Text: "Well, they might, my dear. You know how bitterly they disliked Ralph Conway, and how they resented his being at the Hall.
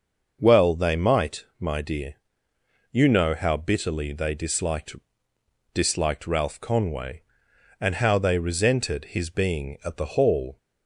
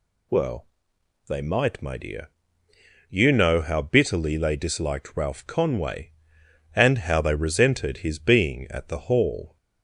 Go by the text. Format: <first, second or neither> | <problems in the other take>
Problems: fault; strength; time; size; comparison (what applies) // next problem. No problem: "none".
second | starts louder than the rest; noticeable; until 1.4 s; 6 dB // says "disliked" twice; at 5.7 s